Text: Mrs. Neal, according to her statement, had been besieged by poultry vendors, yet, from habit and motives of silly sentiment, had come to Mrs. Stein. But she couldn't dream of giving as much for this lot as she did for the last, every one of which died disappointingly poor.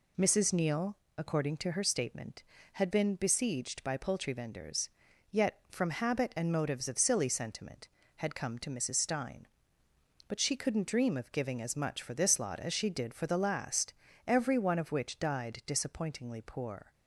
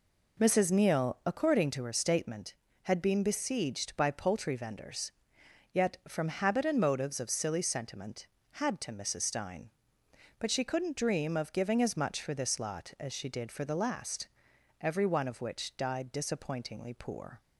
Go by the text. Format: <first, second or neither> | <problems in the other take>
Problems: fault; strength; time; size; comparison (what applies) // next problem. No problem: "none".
first | skips "come"; at 8.8 s